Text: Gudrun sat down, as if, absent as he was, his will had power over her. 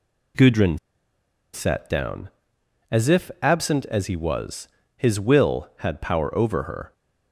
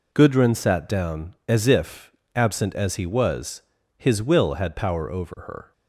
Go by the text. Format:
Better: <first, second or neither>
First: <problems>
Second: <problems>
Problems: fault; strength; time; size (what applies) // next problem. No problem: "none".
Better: second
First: pauses between "Gudrun" and "sat"; noticeable; at 0.7 s; 0.77 s long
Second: none